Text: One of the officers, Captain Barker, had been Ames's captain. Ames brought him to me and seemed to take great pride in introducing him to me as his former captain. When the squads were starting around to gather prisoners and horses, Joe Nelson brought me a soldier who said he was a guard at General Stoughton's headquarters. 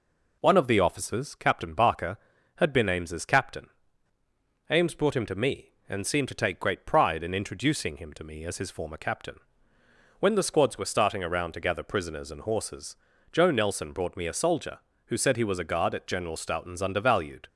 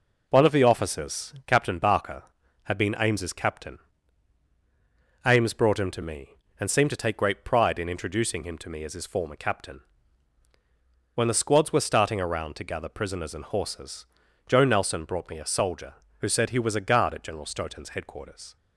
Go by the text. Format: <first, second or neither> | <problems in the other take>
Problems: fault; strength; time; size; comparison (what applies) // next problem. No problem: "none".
second | says "undervalued" for "headquarters"; at 16.8 s